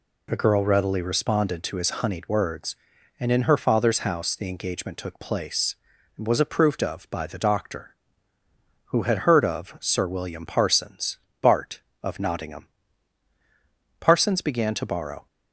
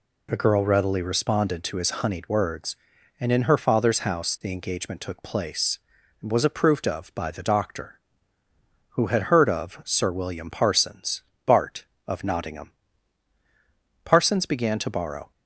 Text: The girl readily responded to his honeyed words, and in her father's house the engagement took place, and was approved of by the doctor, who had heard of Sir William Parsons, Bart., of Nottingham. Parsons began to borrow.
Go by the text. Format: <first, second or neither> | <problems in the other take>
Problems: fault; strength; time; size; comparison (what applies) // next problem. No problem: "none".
neither | none